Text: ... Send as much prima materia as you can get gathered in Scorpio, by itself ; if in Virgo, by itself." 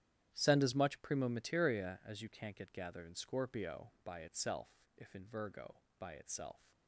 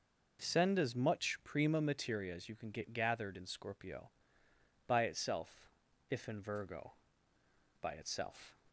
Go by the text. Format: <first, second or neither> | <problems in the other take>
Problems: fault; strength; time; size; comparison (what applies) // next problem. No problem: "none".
second | starts louder than the rest; strong; until 1.3 s; 11 dB // says "can't" for "can"; at 2.2 s